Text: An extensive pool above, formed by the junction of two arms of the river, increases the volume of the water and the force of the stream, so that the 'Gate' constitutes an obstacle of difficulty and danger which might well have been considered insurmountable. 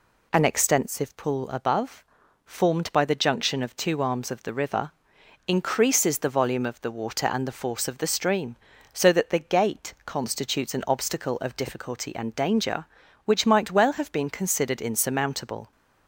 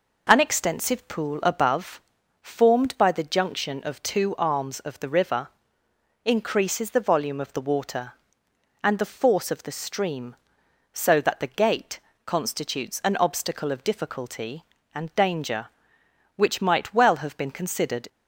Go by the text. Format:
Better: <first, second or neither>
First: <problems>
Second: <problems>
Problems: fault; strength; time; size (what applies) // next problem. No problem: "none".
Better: first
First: none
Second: pauses between "Gate" and "constitutes"; slight; at 11.9 s; 0.26 s long // stops before "insurmountable"; at 18.0 s